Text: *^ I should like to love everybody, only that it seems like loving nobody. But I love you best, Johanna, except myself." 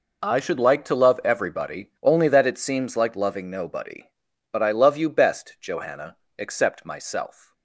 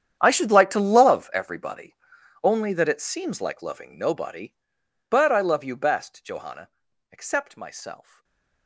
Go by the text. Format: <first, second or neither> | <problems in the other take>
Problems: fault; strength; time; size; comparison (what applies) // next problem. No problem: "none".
first | gets quieter; strong; throughout; 19 dB // stays silent after the last word; slight; from 8.0 s on; 0.6 s long